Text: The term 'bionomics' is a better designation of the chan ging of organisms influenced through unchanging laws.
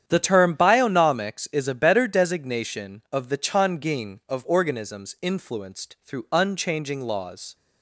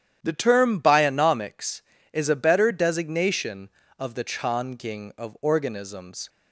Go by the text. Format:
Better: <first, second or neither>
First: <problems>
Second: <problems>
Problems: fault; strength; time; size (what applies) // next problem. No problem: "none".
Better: first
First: starts louder than the rest; strong; until 1.0 s; 9 dB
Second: starts louder than the rest; strong; until 1.2 s; 10.5 dB // stops before "influenced through unchanging laws"; at 6.2 s